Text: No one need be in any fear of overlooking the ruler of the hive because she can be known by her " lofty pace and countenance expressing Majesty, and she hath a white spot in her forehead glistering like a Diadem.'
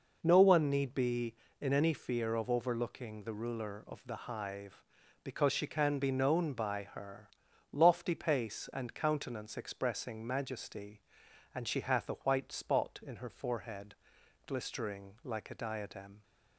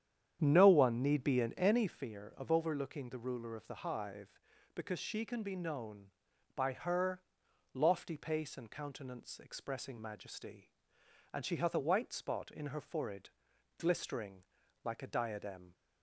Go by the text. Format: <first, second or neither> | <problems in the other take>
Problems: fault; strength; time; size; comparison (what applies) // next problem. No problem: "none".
first | starts louder than the rest; strong; until 2.0 s; 9.5 dB // pauses between "forehead" and "glistering"; noticeable; at 13.2 s; 0.50 s long; noticeable in the first // pauses between "glistering" and "like"; at 14.4 s; 0.40 s long